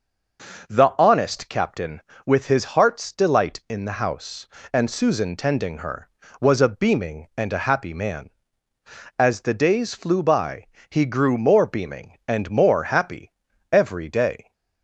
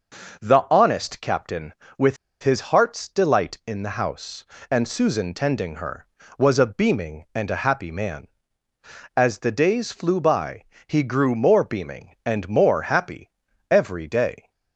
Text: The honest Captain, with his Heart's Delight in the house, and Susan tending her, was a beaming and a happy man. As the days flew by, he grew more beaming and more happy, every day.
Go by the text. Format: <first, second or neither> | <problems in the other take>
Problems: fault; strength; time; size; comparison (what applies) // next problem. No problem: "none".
first | pauses between "with" and "his"; slight; at 2.1 s; 0.26 s long